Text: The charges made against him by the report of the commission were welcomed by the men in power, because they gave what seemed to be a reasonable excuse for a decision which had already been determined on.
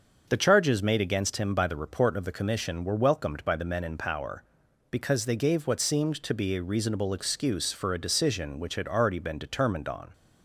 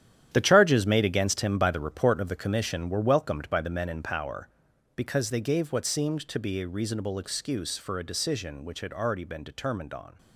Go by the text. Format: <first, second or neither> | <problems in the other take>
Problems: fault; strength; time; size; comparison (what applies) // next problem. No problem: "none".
first | gets quieter; strong; throughout; 10.5 dB // starts louder than the rest; strong; until 1.3 s; 11 dB; also in the first